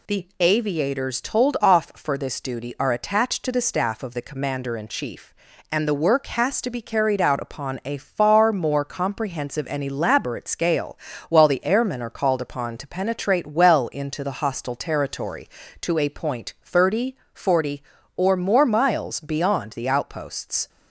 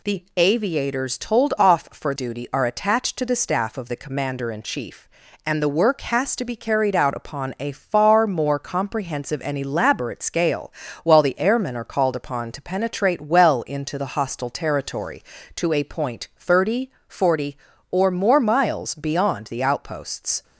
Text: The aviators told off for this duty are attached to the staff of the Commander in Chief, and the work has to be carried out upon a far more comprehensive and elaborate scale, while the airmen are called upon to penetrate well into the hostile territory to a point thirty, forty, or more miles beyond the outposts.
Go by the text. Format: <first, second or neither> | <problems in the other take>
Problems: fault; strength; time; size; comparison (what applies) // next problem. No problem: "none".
first | skips "this"; at 2.1 s